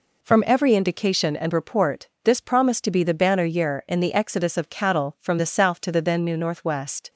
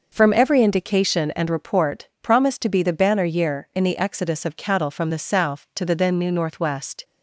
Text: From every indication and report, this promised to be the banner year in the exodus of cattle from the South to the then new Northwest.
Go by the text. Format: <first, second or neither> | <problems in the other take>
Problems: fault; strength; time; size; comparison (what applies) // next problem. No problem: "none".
first | skips "this"; at 2.1 s